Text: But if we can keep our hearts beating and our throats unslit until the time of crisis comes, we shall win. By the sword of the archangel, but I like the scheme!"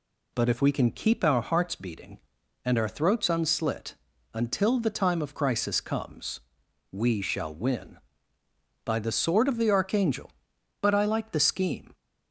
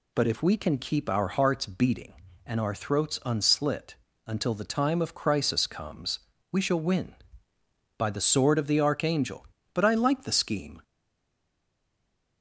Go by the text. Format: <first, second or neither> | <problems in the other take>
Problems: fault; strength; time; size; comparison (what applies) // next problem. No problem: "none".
first | pauses between "unslit" and "until"; slight; at 3.9 s; 0.32 s long; also in the first // stays silent after the last word; noticeable; from 10.8 s on; 1.6 s long